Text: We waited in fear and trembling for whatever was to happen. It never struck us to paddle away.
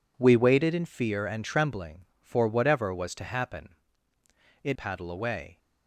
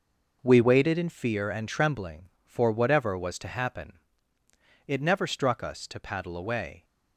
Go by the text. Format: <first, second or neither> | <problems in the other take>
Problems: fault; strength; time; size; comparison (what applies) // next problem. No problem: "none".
second | skips "never struck us to"; at 4.7 s